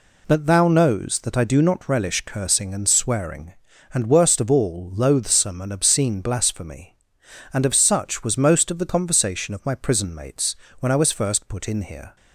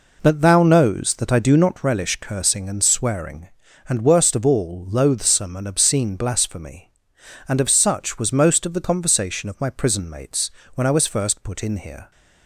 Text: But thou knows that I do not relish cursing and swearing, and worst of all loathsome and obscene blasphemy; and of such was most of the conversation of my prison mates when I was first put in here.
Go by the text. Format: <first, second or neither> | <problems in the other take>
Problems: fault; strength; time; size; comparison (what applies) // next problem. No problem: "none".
first | starts louder than the rest; noticeable; until 1.9 s; 4 dB // pauses between "mates" and "when"; slight; at 10.5 s; 0.24 s long; slight in the first